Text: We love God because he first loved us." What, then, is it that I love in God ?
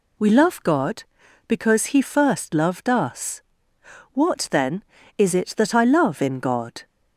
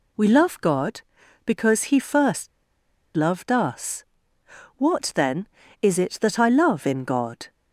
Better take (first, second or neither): first